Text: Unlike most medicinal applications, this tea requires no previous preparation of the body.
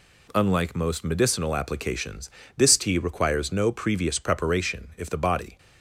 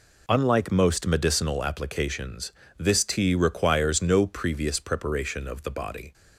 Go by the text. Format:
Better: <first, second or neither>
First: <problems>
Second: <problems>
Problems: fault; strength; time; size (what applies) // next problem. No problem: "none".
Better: second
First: says "if" for "of"; at 4.9 s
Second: none